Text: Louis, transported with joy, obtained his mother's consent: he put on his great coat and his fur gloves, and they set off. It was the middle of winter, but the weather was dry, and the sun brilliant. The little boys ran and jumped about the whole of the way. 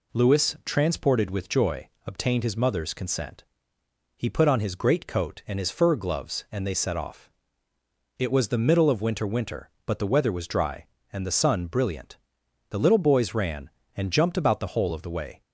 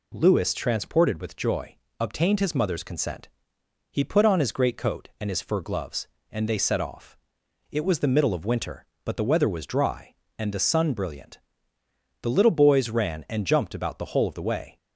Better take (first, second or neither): second